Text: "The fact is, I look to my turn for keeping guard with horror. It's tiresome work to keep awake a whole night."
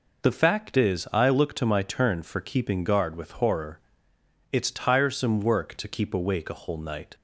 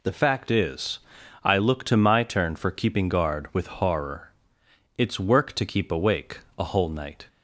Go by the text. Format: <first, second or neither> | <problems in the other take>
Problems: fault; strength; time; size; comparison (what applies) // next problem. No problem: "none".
first | skips "tiresome"; at 5.2 s // pauses between "awake" and "a"; slight; at 6.4 s; 0.16 s long